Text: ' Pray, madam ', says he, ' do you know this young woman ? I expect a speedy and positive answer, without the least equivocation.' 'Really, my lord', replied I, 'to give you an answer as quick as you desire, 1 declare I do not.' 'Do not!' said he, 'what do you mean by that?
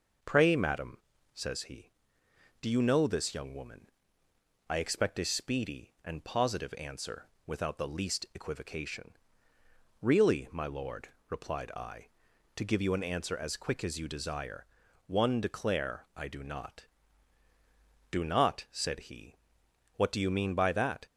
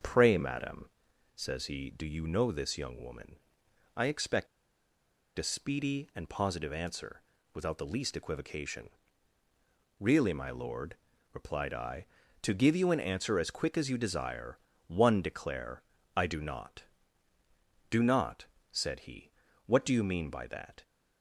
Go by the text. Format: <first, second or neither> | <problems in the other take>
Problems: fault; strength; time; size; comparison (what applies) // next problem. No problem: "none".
first | starts louder than the rest; until 1.2 s; 6.5 dB // pauses between "expect" and "a"; noticeable; at 4.4 s; 0.91 s long // pauses between "declare" and "I"; slight; at 15.8 s; 0.32 s long